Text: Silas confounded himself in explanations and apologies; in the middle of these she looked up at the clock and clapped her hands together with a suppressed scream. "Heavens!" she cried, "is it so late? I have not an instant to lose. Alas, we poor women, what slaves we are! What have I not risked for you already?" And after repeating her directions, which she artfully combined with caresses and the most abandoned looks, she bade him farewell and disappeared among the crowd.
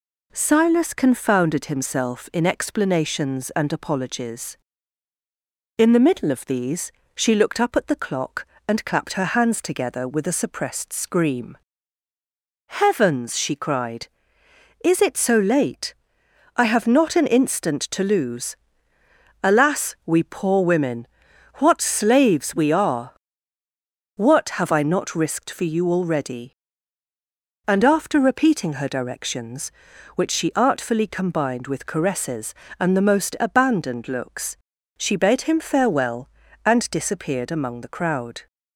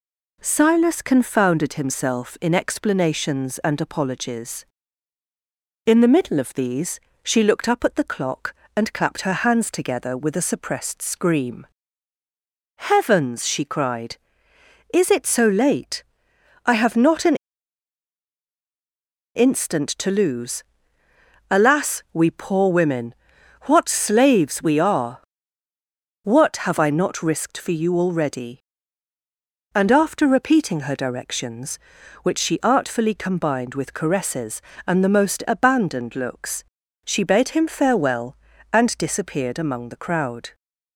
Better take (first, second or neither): first